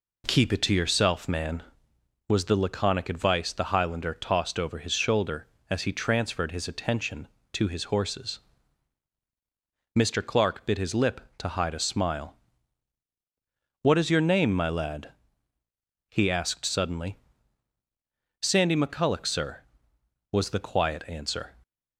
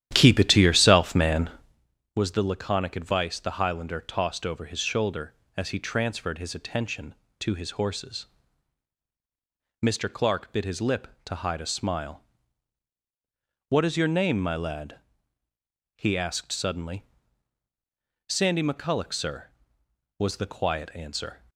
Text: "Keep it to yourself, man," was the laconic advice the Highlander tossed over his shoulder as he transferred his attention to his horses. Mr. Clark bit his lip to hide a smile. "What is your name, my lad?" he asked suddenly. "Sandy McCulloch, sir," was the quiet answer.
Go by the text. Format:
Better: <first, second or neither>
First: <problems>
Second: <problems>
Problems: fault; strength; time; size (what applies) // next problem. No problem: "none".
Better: first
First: none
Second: starts louder than the rest; strong; until 1.9 s; 11.5 dB